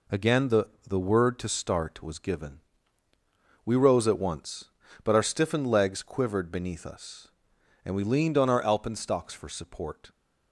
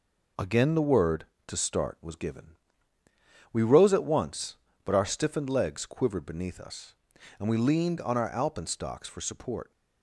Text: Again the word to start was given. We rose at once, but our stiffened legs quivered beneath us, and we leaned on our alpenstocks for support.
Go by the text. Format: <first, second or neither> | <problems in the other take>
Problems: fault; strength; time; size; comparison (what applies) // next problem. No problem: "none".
second | says "the" twice; at 0.8 s